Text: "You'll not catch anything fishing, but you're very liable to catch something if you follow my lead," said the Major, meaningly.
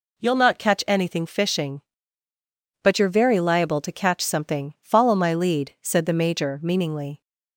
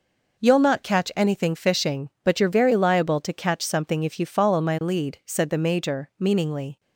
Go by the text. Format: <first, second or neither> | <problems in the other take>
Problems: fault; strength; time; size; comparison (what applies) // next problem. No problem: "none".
second | skips "if you"; at 4.7 s